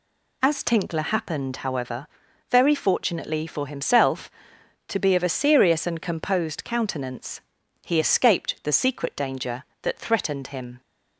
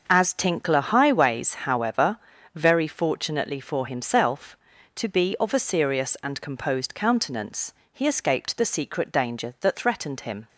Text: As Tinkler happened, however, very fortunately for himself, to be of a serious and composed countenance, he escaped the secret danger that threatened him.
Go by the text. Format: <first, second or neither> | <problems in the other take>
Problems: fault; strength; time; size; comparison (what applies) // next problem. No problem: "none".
first | starts louder than the rest; until 1.1 s; 6 dB // says "highways" for "happened"; at 0.8 s